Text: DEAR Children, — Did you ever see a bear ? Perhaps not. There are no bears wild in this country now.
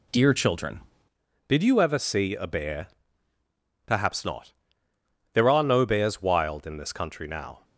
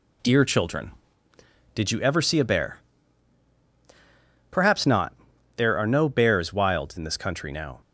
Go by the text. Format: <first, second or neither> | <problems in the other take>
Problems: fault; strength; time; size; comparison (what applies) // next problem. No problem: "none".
second | changes voice at "Did"; from 1.4 s on; 6.2 s long